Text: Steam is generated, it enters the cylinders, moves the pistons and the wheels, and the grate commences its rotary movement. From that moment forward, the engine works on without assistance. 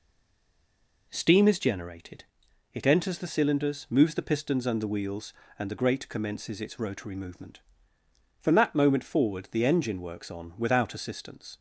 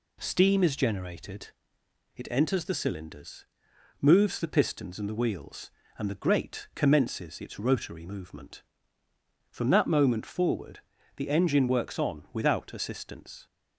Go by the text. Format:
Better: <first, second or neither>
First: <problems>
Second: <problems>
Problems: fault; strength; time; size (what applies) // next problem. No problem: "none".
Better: second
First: stays silent before the first word; until 1.1 s; 1.1 s long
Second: none